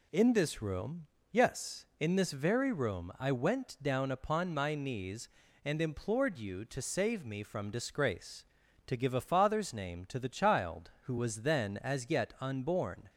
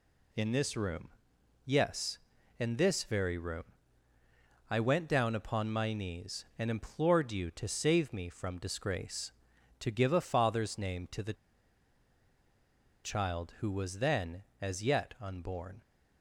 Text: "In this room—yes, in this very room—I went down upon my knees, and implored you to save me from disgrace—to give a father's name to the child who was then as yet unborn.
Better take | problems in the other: first | pauses between "the" and "child"; strong; at 11.3 s; 1.7 s long

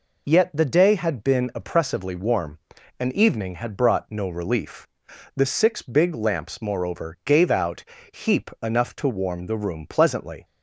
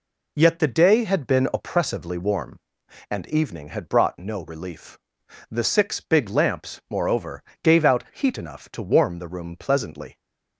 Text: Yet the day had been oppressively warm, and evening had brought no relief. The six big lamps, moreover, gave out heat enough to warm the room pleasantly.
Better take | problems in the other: second | says "heap" for "heat"; at 8.1 s

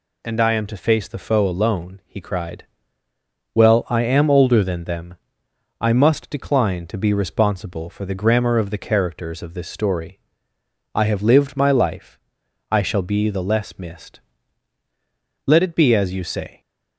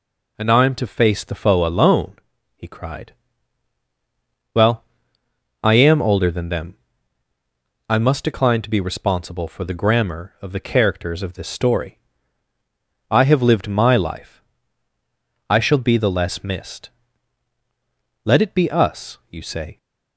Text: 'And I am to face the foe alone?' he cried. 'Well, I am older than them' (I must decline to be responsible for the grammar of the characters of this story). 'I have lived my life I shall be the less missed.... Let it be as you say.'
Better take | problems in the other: first | pauses between "life" and "I"; at 14.4 s; 1.0 s long; noticeable in the first // says "us" for "as"; at 18.7 s

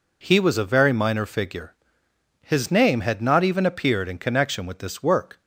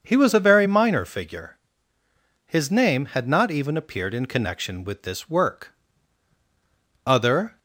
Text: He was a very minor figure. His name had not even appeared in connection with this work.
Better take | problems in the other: first | starts louder than the rest; until 1.0 s; 6.5 dB // goes on to say "Other"; from 7.0 s on; 0.54 s long

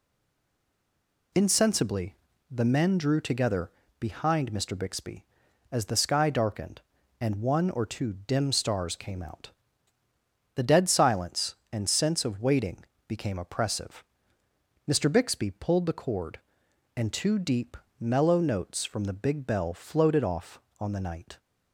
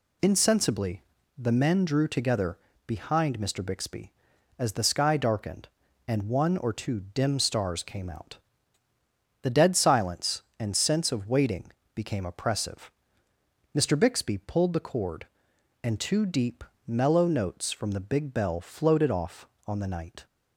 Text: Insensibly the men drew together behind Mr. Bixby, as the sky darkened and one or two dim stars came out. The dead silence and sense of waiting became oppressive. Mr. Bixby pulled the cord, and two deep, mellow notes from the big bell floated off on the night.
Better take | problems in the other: second | stays silent before the first word; noticeable; until 1.3 s; 1.3 s long // pauses between "Insensibly" and "the"; slight; at 2.1 s; 0.34 s long; slight in the second // pauses between "together" and "behind"; slight; at 3.7 s; 0.28 s long; slight in the second // pauses between "waiting" and "became"; slight; at 12.8 s; 0.24 s long; slight in the second

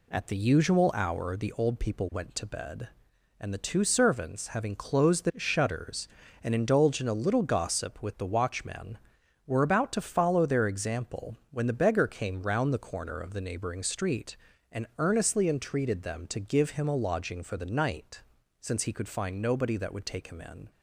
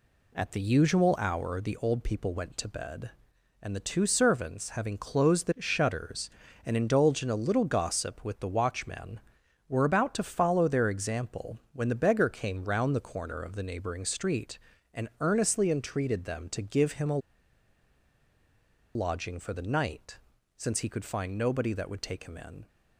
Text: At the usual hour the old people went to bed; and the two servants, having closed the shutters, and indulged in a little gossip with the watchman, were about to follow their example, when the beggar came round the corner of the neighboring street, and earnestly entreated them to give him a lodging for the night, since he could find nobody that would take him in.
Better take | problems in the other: first | pauses between "a" and "lodging"; strong; at 17.1 s; 1.7 s long

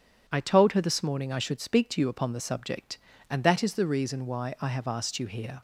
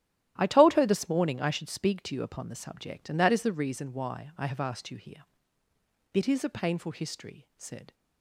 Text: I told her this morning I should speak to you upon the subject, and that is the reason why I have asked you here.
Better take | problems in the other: first | starts louder than the rest; strong; until 1.3 s; 12.5 dB // goes on to say "It is a painful history said"; strong; from 6.1 s on; 1.8 s long

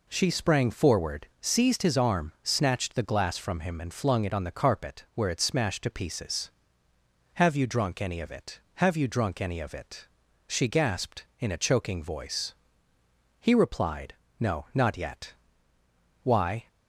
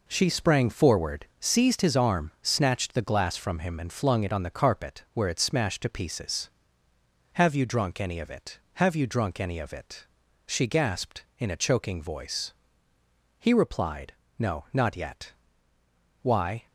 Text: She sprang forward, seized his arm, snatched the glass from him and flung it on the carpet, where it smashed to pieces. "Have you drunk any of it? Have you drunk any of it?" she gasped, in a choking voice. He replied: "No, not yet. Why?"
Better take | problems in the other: first | gets quieter; strong; throughout; 7.5 dB

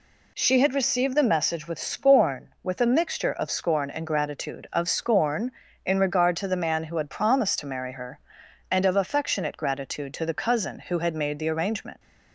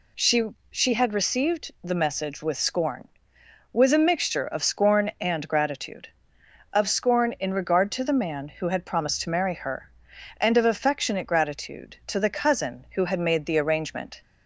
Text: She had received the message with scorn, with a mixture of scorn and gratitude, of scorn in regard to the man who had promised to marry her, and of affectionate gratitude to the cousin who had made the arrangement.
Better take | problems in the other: first | says "She" twice; at 0.7 s

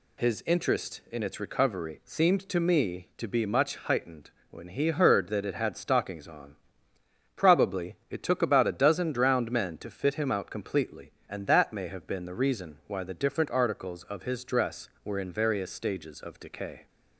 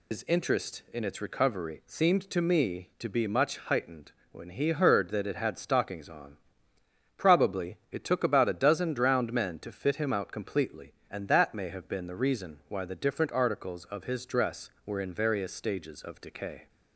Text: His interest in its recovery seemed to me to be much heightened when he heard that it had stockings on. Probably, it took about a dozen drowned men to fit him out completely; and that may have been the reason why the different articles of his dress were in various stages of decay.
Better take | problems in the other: first | loses the start of "His"; at 0.1 s; 115 ms // pauses between "heightened" and "when"; slight; at 4.1 s; 0.20 s long; slight in the first

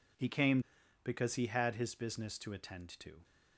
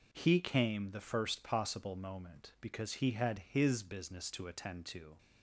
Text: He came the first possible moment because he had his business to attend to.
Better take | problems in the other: second | skips "the first possible moment"; at 0.8 s

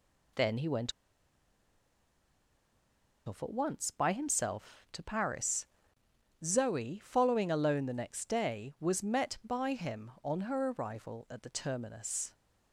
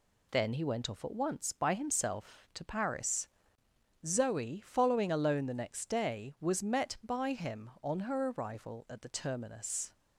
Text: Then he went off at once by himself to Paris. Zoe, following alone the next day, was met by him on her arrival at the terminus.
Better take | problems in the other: second | pauses between "went" and "off"; strong; at 0.9 s; 2.3 s long

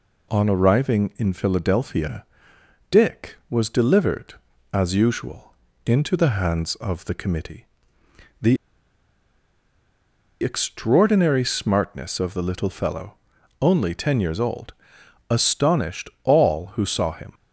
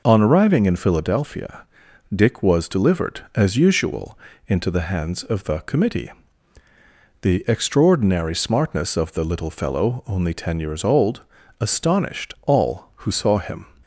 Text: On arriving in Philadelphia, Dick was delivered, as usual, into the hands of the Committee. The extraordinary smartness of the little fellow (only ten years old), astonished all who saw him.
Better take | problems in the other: second | pauses between "The" and "extraordinary"; strong; at 8.5 s; 1.8 s long

